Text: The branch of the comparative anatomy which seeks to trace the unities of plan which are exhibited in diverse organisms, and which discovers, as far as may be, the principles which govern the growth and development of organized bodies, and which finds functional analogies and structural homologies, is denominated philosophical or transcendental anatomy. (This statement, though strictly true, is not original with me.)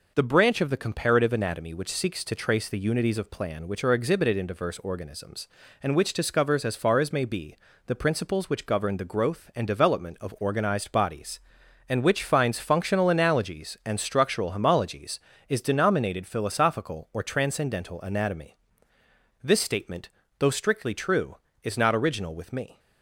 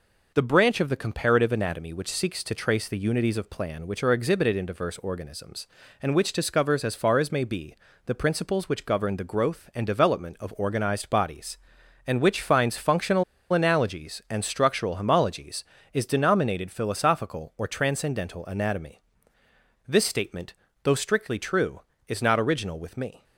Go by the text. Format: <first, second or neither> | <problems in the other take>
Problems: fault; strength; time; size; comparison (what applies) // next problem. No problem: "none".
first | pauses between "functional" and "analogies"; slight; at 13.2 s; 0.29 s long